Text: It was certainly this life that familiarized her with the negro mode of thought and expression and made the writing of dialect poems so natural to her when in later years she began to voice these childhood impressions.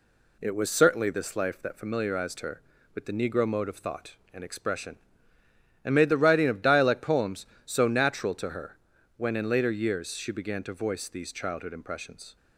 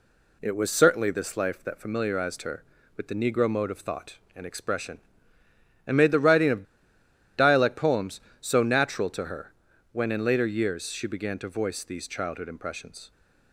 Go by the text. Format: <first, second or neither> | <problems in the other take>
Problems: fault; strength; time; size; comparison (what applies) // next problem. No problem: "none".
first | pauses between "of" and "dialect"; noticeable; at 6.6 s; 0.75 s long // pauses between "her" and "when"; at 9.5 s; 0.38 s long; also in the first